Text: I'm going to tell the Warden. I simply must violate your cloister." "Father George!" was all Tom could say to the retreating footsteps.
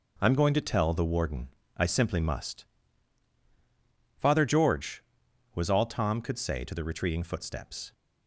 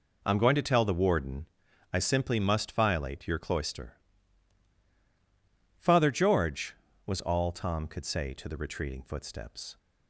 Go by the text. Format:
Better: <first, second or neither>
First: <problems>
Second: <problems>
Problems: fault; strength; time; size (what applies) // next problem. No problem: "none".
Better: second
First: skips "violate your cloister"; at 3.4 s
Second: none